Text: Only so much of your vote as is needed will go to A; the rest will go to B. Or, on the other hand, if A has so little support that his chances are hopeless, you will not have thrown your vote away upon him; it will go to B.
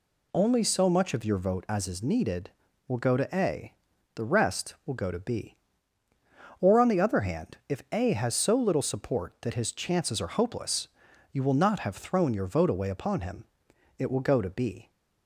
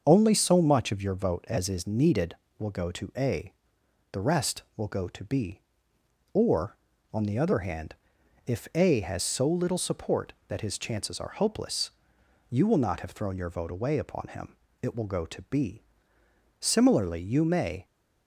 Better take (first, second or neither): first